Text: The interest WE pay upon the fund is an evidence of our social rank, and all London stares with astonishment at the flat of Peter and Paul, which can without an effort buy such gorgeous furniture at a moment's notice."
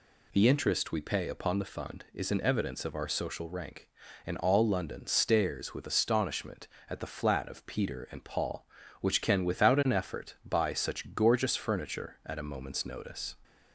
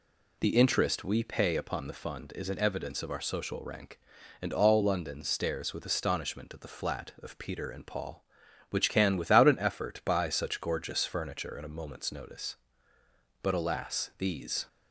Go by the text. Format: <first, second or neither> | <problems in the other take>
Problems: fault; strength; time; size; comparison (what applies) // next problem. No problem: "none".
first | goes on to say "But alas these"; noticeable; from 13.4 s on; 1.2 s long